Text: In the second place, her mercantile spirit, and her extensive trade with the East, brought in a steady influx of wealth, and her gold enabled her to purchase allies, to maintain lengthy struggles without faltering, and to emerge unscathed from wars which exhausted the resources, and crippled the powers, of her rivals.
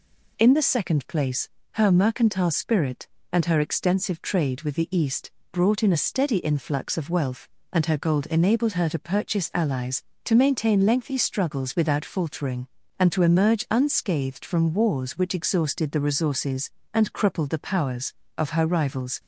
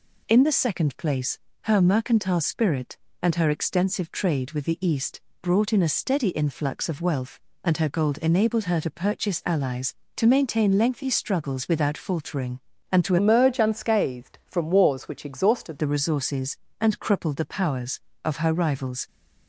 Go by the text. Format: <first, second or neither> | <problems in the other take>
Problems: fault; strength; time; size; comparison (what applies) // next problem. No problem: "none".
first | changes voice from "emerge" to "exhausted"; from 13.1 to 15.7 s; 2.6 s long